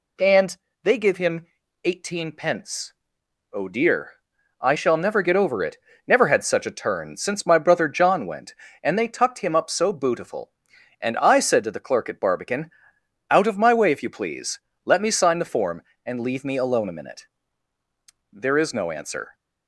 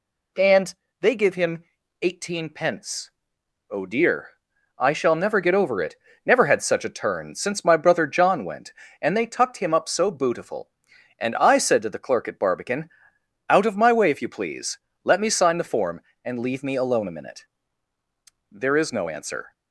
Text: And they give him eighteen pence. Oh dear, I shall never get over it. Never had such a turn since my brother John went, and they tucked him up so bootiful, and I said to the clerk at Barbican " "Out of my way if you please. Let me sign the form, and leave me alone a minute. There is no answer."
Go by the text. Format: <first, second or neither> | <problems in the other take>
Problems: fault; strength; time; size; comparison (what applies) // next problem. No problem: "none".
neither | pauses between "And" and "they"; slight; the same in both // pauses between "him" and "eighteen"; the same in both